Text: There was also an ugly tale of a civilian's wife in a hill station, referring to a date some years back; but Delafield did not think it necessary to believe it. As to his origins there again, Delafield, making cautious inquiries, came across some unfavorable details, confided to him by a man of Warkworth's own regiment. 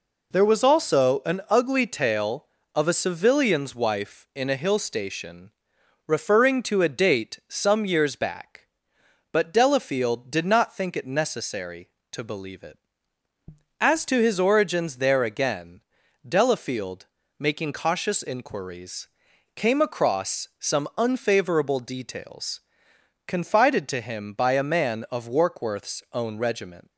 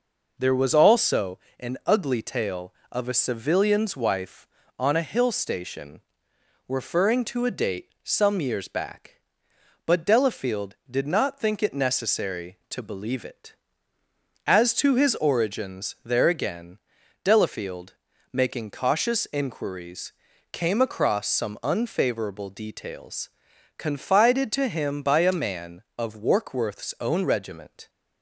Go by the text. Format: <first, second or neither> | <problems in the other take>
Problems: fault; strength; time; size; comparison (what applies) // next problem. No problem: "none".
first | pauses between "also" and "an"; slight; at 1.3 s; 0.20 s long // says "on" for "in"; at 4.7 s